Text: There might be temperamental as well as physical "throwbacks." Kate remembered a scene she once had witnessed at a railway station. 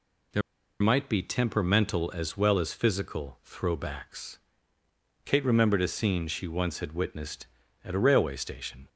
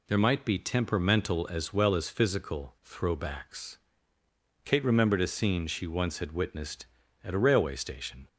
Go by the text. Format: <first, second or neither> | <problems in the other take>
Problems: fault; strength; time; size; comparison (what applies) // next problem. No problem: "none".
second | pauses between "There" and "might"; at 0.4 s; 0.40 s long